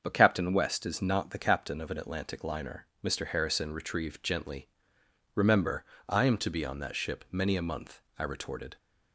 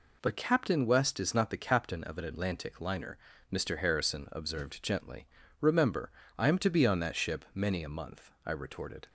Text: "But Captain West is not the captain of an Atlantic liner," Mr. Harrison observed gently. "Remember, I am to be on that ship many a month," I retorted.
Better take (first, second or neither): second